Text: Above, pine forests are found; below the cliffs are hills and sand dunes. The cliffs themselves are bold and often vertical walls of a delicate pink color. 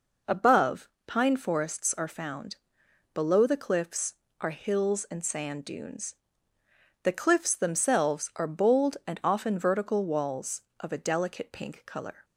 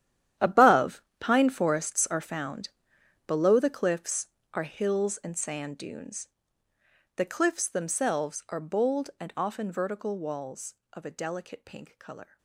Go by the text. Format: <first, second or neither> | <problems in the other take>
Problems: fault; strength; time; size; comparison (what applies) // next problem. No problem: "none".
first | gets quieter; strong; throughout; 15 dB